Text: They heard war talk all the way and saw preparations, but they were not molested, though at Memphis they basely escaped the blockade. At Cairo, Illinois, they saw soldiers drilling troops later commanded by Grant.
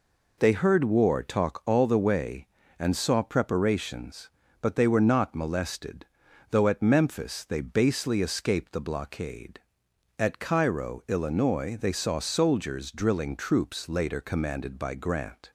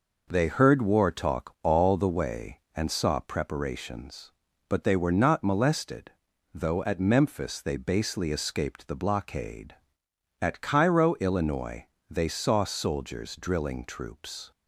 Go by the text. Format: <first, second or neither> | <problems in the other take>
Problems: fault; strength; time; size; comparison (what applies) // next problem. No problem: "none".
first | stops before "later commanded by Grant"; at 14.5 s